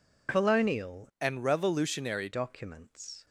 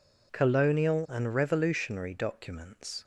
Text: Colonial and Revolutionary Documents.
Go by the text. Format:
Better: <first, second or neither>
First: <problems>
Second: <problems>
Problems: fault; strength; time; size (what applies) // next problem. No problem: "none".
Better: second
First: changes voice from "and" to "Revolutionary"; from 1.1 to 2.2 s; 1.1 s long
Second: none